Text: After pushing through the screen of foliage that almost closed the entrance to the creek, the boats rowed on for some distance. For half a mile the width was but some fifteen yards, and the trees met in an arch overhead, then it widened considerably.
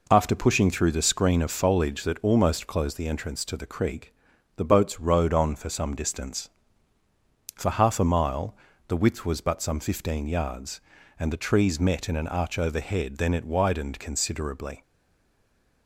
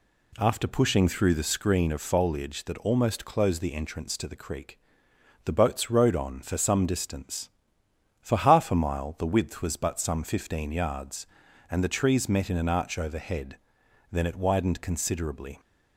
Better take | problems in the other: second | pauses between "mile" and "the"; slight; at 8.5 s; 0.32 s long // stays silent after the last word; from 14.8 s on; 1.0 s long

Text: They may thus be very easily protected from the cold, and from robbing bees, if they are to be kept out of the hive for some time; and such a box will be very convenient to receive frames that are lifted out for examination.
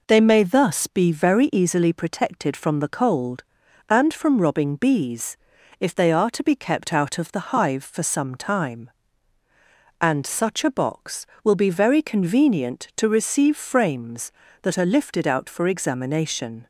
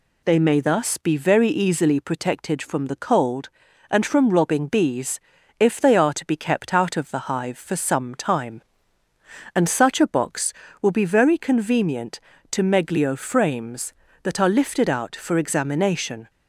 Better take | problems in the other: first | says "meglio" for "receive"; at 12.6 s

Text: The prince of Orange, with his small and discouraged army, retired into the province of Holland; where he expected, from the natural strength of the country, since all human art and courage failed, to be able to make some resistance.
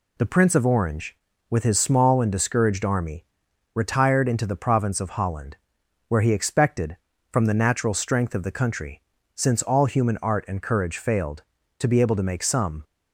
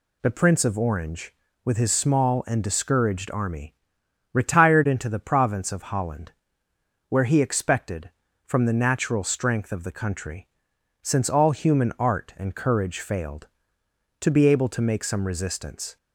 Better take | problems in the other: second | stops before "resistance"; at 12.8 s

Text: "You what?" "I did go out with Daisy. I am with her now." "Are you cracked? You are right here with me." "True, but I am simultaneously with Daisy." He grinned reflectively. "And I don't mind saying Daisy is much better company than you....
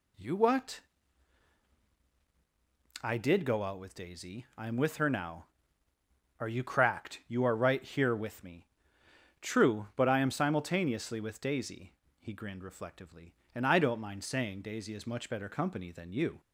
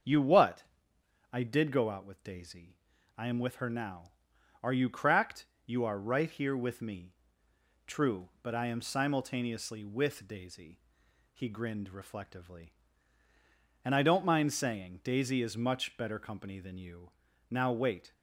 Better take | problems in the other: first | starts louder than the rest; until 1.7 s; 6.5 dB // goes on to say "Now wait"; noticeable; from 17.4 s on; 0.64 s long

